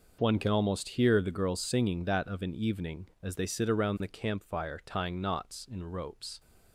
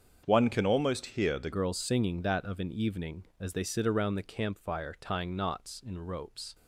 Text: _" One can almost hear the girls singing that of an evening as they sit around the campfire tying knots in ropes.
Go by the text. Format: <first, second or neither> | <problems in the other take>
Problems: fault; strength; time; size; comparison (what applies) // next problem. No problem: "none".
first | starts louder than the rest; until 1.2 s; 7 dB // changes voice from "One" to "the"; from 0.2 to 1.5 s; 1.3 s long